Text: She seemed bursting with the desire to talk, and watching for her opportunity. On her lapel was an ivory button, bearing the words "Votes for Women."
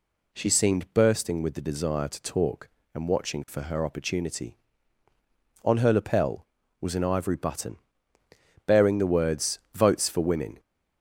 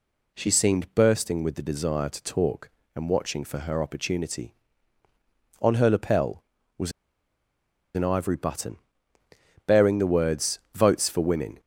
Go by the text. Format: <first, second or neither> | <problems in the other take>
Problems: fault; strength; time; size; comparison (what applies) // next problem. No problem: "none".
first | pauses between "was" and "an"; at 6.9 s; 1.0 s long